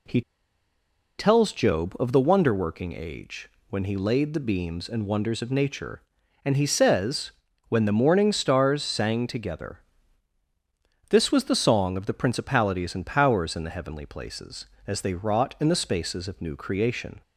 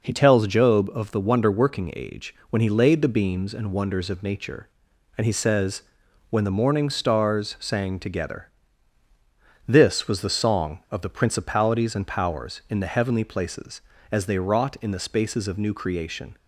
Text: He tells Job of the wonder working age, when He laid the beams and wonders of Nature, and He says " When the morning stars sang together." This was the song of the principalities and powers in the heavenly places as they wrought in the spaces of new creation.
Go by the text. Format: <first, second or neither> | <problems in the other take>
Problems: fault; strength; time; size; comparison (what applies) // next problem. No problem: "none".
second | pauses between "He" and "tells"; noticeable; at 0.2 s; 0.97 s long